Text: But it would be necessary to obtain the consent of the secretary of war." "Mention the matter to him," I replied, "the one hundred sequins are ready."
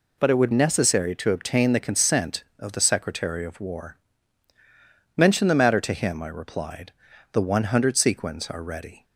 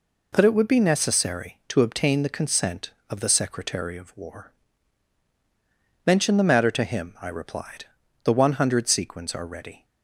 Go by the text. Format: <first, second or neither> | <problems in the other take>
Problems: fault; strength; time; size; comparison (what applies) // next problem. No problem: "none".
second | skips "be"; at 0.5 s